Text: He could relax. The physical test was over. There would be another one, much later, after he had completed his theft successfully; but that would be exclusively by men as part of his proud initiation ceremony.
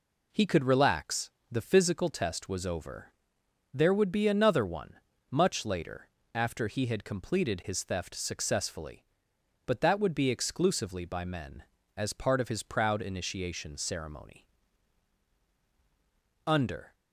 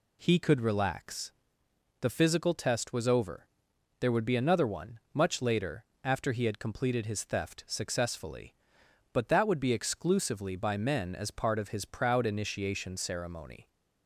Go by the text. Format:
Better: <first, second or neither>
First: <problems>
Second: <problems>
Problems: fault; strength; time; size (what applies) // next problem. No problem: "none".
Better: second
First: goes on to say "Under"; slight; from 16.4 s on; 0.48 s long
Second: none